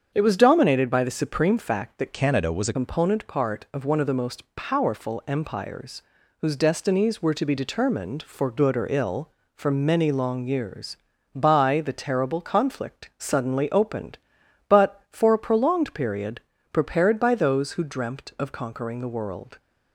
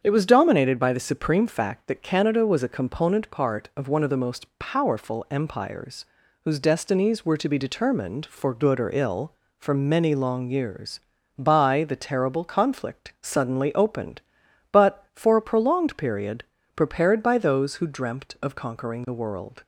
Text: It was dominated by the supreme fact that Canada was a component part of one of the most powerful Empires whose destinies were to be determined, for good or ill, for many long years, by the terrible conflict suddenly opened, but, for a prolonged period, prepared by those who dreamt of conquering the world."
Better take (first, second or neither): second